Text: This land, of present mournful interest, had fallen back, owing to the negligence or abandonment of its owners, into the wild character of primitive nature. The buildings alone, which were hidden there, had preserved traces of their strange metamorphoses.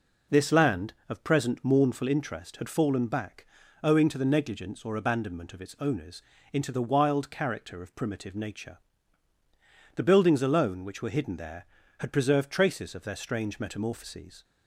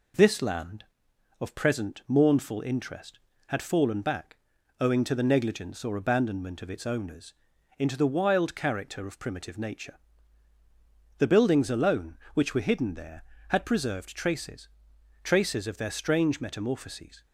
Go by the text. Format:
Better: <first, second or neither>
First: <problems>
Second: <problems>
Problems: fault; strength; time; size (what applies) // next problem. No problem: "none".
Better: first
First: none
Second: says "traces" twice; at 15.2 s